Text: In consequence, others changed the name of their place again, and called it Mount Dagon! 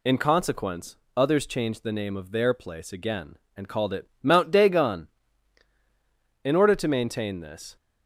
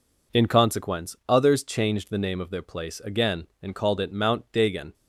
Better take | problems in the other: second | goes on to say "In order to maintain this"; from 6.4 s on; 1.3 s long

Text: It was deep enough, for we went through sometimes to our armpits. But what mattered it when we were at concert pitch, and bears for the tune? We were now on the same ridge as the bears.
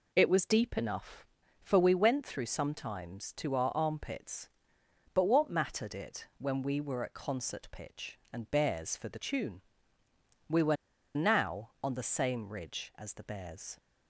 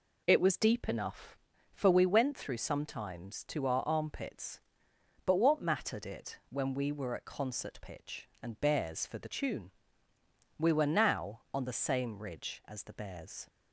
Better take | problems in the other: second | pauses between "were" and "now"; at 10.7 s; 0.39 s long

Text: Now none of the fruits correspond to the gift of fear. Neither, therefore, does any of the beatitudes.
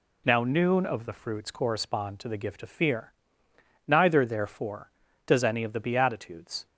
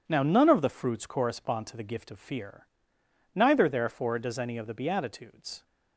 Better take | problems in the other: second | says "noon" for "none"; at 0.4 s

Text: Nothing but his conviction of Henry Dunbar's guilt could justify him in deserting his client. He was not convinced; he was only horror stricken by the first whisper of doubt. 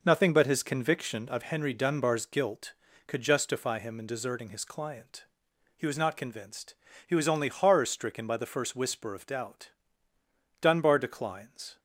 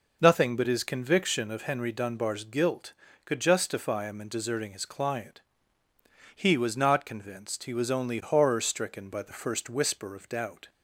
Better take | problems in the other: second | goes on to say "Dunbar declines"; noticeable; from 10.6 s on; 1.1 s long

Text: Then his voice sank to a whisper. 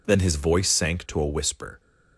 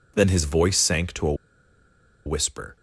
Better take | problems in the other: first | pauses between "a" and "whisper"; noticeable; at 1.3 s; 0.91 s long

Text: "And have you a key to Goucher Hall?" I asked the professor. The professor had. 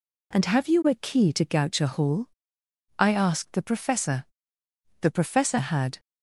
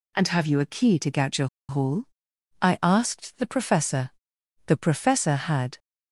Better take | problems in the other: first | pauses between "Goucher" and "Hall"; slight; at 1.4 s; 0.22 s long

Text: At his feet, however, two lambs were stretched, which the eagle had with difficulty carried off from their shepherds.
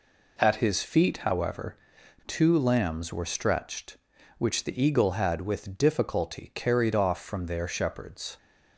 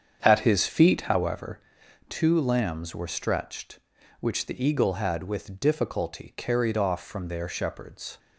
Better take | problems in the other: first | starts louder than the rest; strong; until 1.4 s; 7.5 dB

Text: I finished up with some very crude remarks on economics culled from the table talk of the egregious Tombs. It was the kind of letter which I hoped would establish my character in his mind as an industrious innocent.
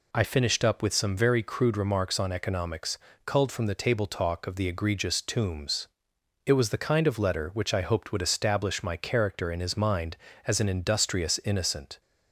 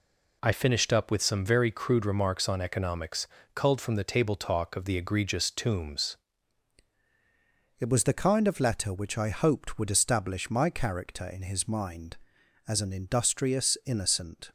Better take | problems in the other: first | pauses between "economics" and "culled"; slight; at 3.2 s; 0.28 s long; slight in the first // changes voice at "It"; from 7.7 s on; 6.8 s long

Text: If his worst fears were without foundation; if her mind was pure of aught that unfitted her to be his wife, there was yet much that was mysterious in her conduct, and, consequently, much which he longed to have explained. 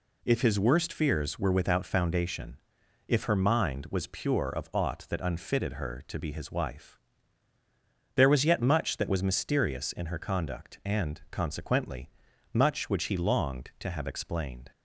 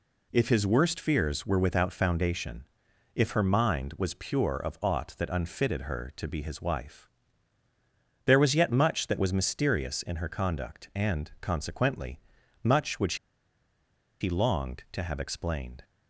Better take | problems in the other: first | pauses between "which" and "he"; at 13.1 s; 1.0 s long

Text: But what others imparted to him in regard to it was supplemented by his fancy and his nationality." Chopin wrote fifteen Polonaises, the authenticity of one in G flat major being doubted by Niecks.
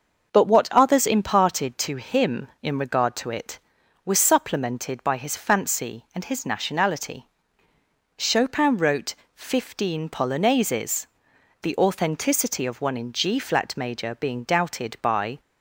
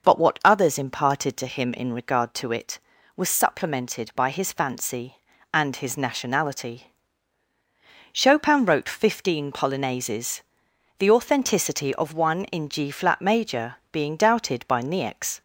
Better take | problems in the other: second | starts louder than the rest; until 1.3 s; 6 dB // pauses between "wrote" and "fifteen"; slight; at 9.1 s; 0.18 s long // stops before "Niecks"; at 15.3 s

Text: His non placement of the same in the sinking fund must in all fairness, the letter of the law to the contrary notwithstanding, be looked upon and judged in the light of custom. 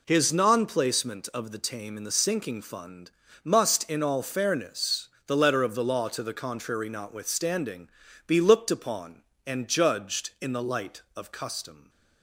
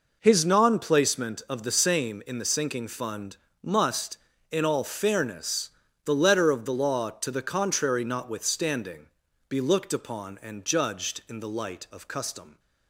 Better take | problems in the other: second | says "tame" for "same"; at 1.5 s // pauses between "fund" and "must"; slight; at 3.0 s; 0.34 s long; slight in the second

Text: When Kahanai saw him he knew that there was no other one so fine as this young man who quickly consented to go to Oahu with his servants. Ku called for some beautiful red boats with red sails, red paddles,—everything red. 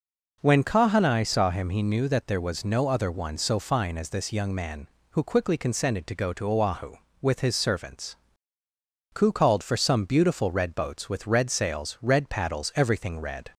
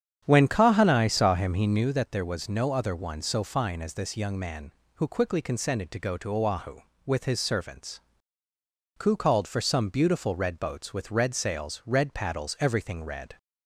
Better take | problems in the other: first | starts louder than the rest; strong; until 2.0 s; 8.5 dB

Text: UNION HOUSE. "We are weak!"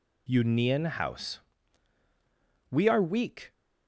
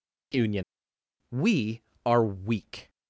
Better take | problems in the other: first | skips "HOUSE"; at 0.9 s

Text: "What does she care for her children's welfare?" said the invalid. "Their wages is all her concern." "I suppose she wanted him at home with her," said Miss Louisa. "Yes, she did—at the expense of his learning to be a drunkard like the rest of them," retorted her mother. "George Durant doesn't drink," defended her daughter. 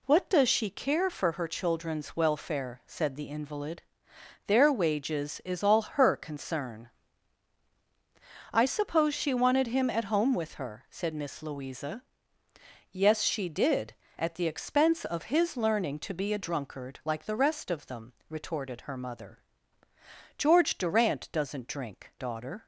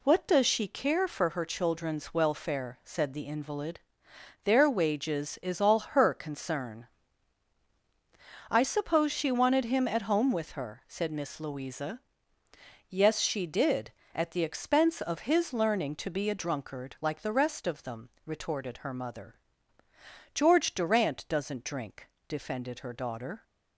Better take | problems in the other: second | skips "defended her"; at 22.1 s

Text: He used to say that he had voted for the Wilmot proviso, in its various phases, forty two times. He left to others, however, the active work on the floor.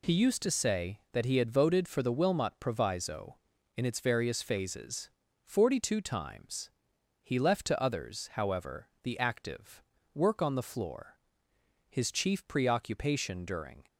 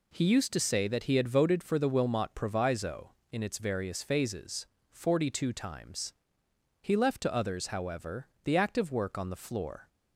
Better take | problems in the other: second | pauses between "active" and "work"; slight; at 9.8 s; 0.30 s long // goes on to say "His chief preoccupation during"; strong; from 11.8 s on; 1.9 s long

